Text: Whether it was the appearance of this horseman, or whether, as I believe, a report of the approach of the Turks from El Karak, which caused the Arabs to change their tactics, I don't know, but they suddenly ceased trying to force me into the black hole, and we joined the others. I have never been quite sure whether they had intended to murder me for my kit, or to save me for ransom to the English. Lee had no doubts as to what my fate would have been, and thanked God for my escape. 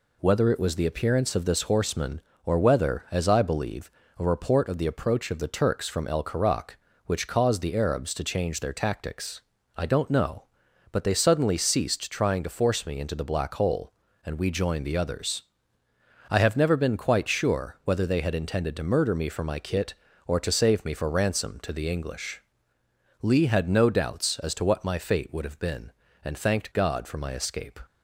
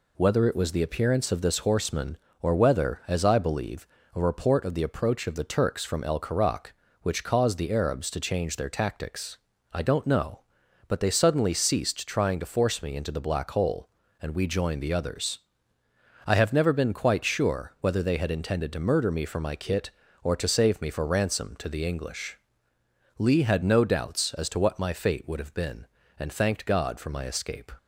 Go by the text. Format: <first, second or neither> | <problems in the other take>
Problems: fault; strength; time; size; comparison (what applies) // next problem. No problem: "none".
neither | none